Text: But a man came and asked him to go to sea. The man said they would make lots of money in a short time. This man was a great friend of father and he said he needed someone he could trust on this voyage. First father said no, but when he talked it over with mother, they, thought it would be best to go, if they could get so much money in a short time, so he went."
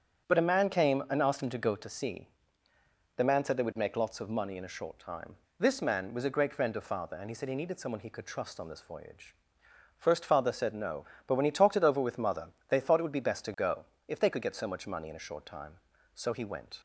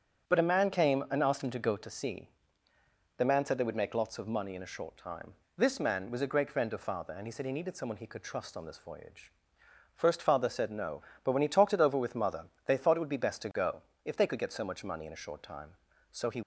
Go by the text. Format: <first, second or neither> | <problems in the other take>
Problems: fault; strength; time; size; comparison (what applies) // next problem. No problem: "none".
first | starts louder than the rest; strong; until 1.3 s; 7.5 dB; strong in the first // stops before "went"; at 16.4 s